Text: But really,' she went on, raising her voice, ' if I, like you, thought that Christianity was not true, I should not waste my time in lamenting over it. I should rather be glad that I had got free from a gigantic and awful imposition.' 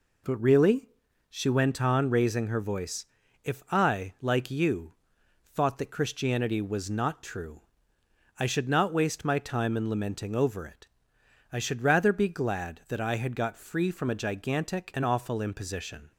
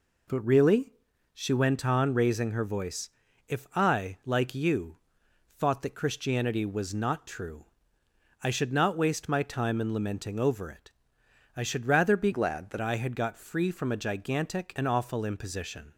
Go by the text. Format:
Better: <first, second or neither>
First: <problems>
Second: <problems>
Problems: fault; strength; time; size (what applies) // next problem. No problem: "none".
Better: first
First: none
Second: changes voice from "glad" to "that"; from 12.3 to 12.7 s; 0.4 s long